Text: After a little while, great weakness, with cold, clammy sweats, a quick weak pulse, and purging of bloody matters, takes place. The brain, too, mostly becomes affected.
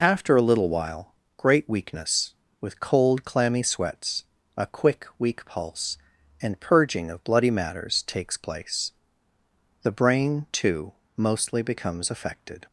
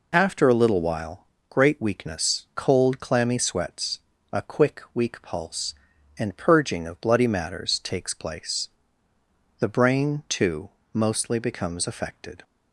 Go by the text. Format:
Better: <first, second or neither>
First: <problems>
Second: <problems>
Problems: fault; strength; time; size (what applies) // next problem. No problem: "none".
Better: first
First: none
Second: skips "with"; at 2.5 s